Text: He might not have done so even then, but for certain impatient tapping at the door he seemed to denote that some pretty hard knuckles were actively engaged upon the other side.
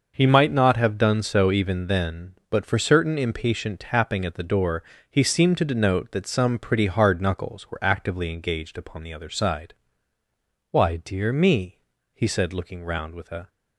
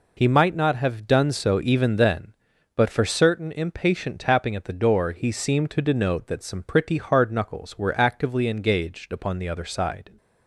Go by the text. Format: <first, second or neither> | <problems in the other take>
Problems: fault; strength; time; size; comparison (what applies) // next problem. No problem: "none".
second | pauses between "door" and "he"; slight; at 4.8 s; 0.30 s long // goes on to say "Why dear me he said looking round with a"; strong; from 10.7 s on; 2.7 s long